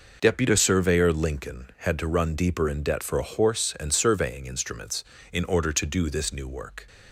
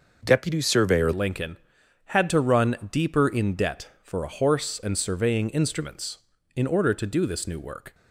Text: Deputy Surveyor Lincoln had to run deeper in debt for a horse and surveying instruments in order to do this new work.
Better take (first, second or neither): first